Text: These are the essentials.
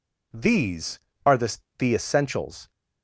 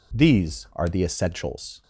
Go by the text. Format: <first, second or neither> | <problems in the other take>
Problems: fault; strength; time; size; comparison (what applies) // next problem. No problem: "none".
second | says "the" twice; at 1.7 s